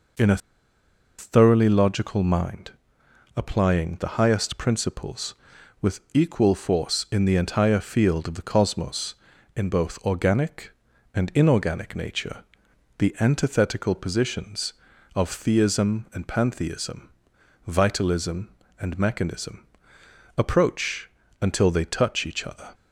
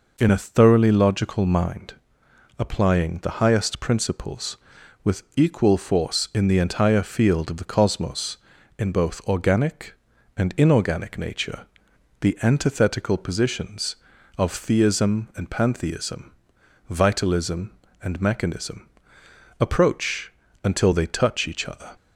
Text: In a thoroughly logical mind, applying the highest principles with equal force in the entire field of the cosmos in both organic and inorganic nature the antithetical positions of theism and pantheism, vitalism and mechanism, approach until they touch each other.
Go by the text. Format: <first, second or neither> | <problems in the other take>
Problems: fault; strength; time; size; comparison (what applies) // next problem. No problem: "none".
second | pauses between "a" and "thoroughly"; noticeable; at 0.3 s; 0.81 s long // pauses between "nature" and "the"; noticeable; at 12.4 s; 0.54 s long; noticeable in the second // pauses between "approach" and "until"; slight; at 21.0 s; 0.32 s long; slight in the second